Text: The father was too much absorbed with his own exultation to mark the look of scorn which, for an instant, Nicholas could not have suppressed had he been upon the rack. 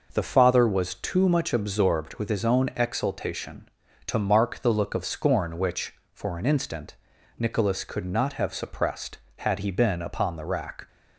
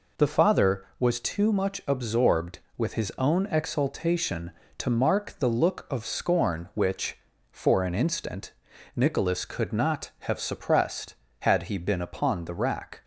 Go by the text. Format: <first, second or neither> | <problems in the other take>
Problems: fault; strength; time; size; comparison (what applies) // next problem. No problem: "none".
neither | none